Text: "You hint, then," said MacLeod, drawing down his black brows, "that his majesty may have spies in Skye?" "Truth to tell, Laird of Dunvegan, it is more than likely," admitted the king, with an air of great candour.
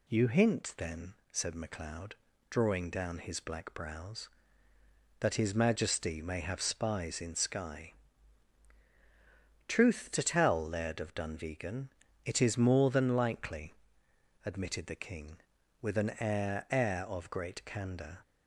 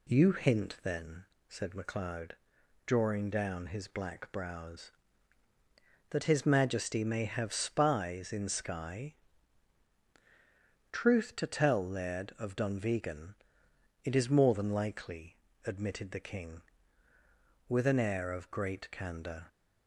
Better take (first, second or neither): second